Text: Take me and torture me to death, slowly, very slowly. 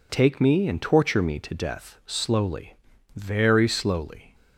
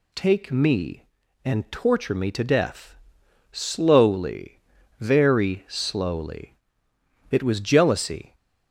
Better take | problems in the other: first | goes on to say "It was jealousy"; noticeable; from 7.3 s on; 1.0 s long

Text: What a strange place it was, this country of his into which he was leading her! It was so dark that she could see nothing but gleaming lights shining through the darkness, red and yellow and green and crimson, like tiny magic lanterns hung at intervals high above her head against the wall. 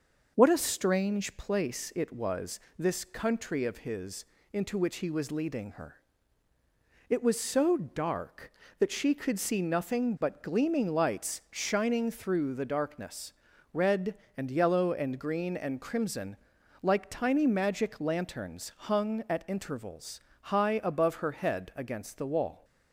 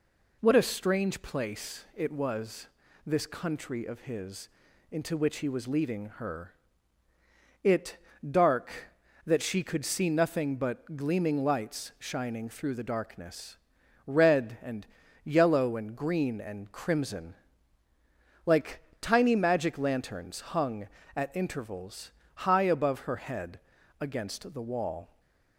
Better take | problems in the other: first | pauses between "his" and "into"; at 4.4 s; 0.42 s long; slight in the first // skips "was so"; at 8.1 s // pauses between "and" and "yellow"; at 14.8 s; 0.40 s long // pauses between "like" and "tiny"; slight; at 18.8 s; 0.21 s long // pauses between "intervals" and "high"; slight; at 22.1 s; 0.22 s long; slight in the first // pauses between "head" and "against"; at 23.5 s; 0.40 s long

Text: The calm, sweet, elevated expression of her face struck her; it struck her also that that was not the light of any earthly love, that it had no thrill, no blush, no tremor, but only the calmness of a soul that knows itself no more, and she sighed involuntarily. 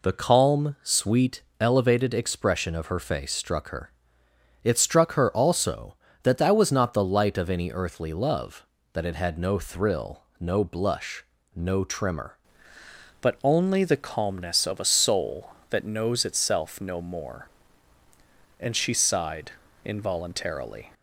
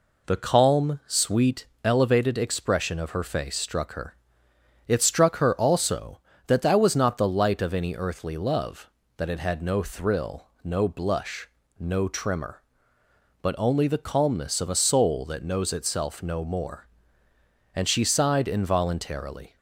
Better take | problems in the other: second | changes voice at "but"; from 13.1 s on; 7.8 s long // pauses between "sighed" and "involuntarily"; slight; at 19.5 s; 0.32 s long

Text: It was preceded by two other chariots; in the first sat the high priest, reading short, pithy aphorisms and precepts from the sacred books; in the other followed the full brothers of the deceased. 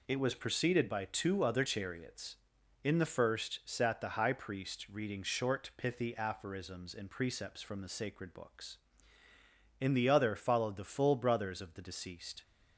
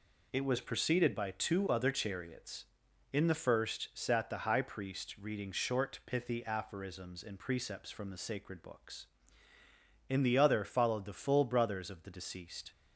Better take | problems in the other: neither | none

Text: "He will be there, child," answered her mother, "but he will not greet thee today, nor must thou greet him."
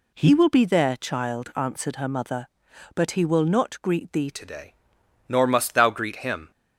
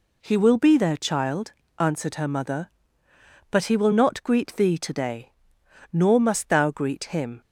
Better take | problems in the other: second | changes voice at "today"; from 4.3 s on; 2.2 s long

